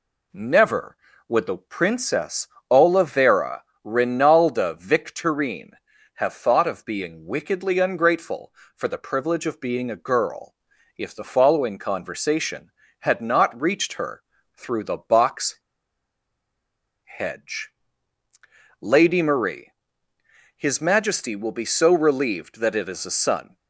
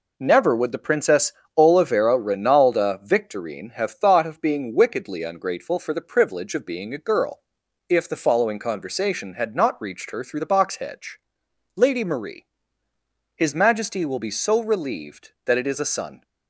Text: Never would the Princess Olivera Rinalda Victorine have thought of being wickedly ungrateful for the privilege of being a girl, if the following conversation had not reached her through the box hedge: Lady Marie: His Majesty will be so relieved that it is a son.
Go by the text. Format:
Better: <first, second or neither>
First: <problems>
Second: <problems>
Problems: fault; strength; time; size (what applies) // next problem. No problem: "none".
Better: second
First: pauses between "Princess" and "Olivera"; slight; at 2.4 s; 0.22 s long // pauses between "Olivera" and "Rinalda"; slight; at 3.6 s; 0.22 s long // pauses between "her" and "through"; slight; at 14.2 s; 0.34 s long // pauses between "box" and "hedge"; strong; at 15.5 s; 1.4 s long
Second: pauses between "Princess" and "Olivera"; slight; at 1.3 s; 0.24 s long